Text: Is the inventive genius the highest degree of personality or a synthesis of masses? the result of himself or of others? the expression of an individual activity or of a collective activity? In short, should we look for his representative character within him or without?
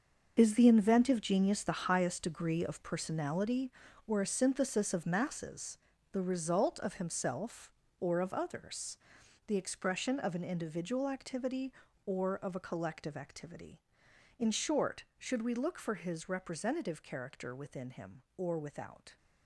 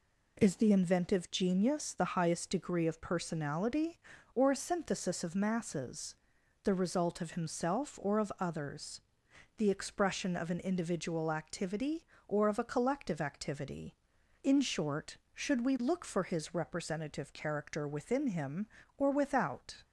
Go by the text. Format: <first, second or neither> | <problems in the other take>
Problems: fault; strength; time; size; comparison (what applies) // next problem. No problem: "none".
second | gets quieter; strong; throughout; 11 dB